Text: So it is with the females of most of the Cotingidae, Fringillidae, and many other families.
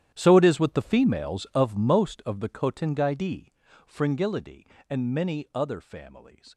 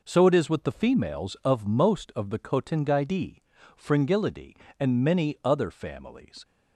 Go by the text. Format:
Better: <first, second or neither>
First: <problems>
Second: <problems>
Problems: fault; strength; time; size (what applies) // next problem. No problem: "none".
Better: second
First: gets quieter; strong; throughout; 16.5 dB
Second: none